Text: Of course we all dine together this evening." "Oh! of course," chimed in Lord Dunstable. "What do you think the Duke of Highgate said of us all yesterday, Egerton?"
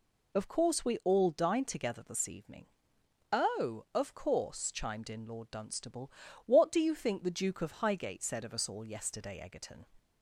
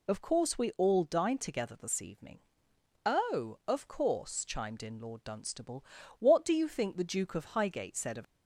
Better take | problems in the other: first | stops before "us all yesterday Egerton"; at 8.2 s

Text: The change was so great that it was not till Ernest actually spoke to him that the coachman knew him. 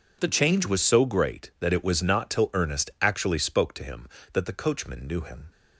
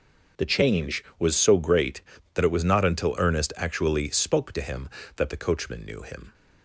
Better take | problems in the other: first | starts louder than the rest; noticeable; until 1.5 s; 6 dB // says "until" for "till"; at 2.8 s

